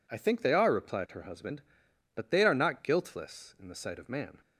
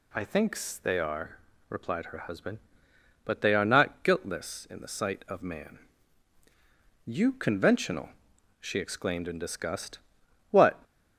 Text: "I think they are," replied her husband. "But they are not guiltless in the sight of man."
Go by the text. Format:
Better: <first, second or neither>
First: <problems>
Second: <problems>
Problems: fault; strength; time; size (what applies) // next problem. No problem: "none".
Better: first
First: none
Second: pauses between "think" and "they"; slight; at 0.5 s; 0.24 s long // goes on to say "You conventional she exclaimed in disgust What"; strong; from 7.0 s on; 3.7 s long